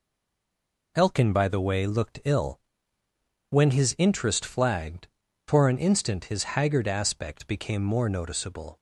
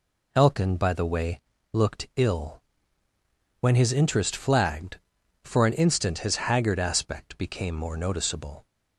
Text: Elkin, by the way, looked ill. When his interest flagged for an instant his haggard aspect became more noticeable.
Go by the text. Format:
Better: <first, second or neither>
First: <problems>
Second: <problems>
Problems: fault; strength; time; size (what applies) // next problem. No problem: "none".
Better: second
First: stays silent before the first word; slight; until 0.9 s; 0.9 s long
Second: none